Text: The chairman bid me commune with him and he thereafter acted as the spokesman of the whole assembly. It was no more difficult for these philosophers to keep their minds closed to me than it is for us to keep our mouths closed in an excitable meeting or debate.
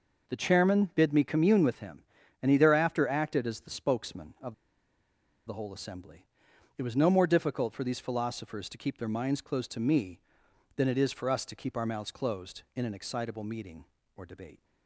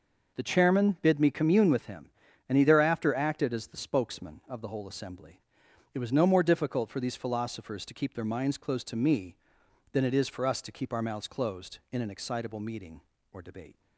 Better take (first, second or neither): second